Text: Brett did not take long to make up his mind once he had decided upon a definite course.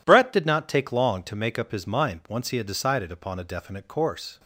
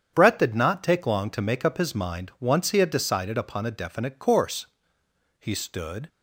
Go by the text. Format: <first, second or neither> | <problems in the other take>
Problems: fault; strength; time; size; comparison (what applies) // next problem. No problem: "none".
first | starts louder than the rest; strong; until 1.1 s; 8 dB // goes on to say "He stood"; noticeable; from 5.4 s on; 0.68 s long